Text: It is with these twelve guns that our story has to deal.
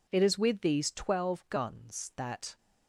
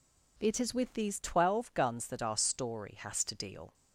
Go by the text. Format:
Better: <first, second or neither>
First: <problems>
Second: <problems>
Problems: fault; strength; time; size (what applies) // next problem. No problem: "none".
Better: second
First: stops before "our story has to deal"; at 2.5 s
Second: none